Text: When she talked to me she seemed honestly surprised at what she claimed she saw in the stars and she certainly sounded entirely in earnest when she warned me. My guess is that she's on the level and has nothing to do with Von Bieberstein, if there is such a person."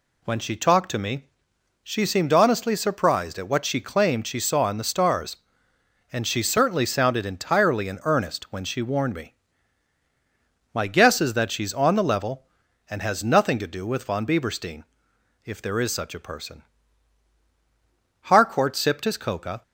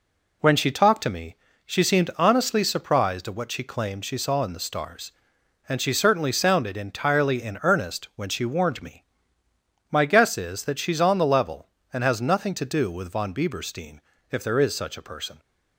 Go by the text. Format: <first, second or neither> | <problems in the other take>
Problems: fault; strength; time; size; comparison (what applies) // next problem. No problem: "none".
second | pauses between "me" and "she"; noticeable; at 1.2 s; 0.60 s long; slight in the second // goes on to say "Harcourt sipped his Coca"; from 18.2 s on; 1.4 s long